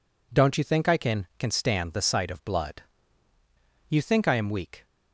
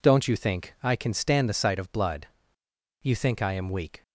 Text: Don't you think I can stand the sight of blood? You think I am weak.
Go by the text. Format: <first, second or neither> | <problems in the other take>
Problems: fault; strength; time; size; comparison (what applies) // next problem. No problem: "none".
second | says "can" twice; at 1.3 s